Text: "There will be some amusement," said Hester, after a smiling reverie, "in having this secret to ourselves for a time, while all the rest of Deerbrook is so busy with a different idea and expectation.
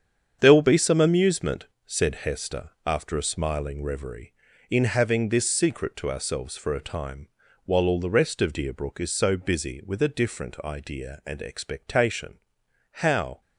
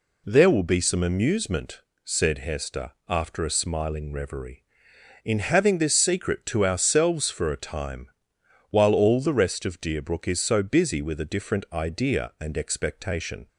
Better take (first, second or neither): second